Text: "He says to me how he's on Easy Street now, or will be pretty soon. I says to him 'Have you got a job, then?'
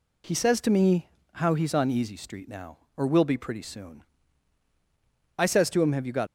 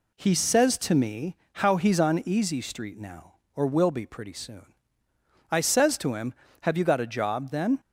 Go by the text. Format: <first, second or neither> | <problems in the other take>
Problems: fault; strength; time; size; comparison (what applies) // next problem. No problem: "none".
second | pauses between "me" and "how"; slight; at 1.0 s; 0.26 s long; slight in the second // stops before "a job then"; at 6.2 s